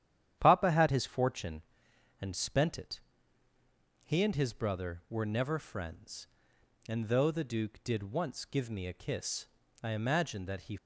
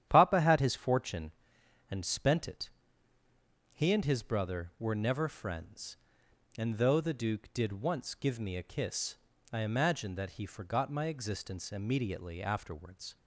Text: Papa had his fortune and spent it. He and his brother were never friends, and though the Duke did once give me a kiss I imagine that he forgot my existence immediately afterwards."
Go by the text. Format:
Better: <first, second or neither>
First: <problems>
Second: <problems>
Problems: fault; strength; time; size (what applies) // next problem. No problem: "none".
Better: second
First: starts louder than the rest; strong; until 1.4 s; 10.5 dB // pauses between "kiss" and "I"; slight; at 9.4 s; 0.36 s long // stops before "forgot my existence immediately afterwards"; at 10.7 s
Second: starts louder than the rest; strong; until 1.1 s; 10 dB // pauses between "kiss" and "I"; slight; at 9.1 s; 0.36 s long